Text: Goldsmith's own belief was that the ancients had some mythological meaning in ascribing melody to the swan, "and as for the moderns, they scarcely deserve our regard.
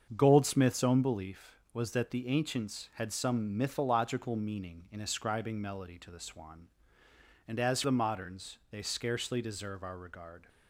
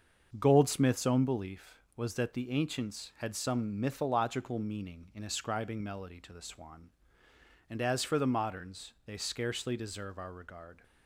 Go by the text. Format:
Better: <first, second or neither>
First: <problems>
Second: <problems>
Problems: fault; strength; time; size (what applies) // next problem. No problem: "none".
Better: second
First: starts louder than the rest; until 1.1 s; 7 dB // skips "for"; at 7.8 s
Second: starts louder than the rest; until 1.4 s; 6.5 dB